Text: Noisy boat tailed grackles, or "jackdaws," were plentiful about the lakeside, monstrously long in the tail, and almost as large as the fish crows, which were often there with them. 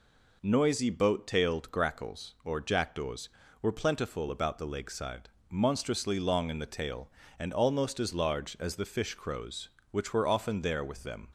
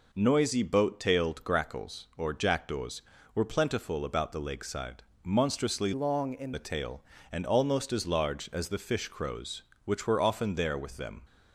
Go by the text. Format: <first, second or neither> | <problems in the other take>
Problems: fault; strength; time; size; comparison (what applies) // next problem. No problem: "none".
first | changes voice from "long" to "in"; from 5.9 to 6.5 s; 0.6 s long